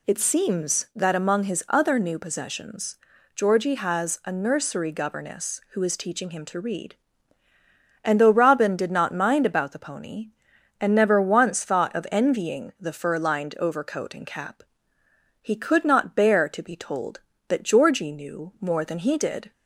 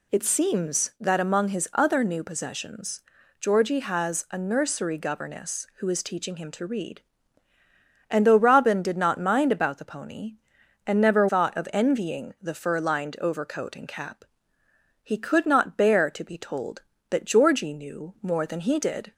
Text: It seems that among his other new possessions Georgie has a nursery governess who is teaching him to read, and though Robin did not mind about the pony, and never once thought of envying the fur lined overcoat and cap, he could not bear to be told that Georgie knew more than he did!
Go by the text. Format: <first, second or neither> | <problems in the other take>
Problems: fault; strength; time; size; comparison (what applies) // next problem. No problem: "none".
first | pauses between "possessions" and "Georgie"; at 3.0 s; 0.38 s long; also in the first // skips "once"; at 11.2 s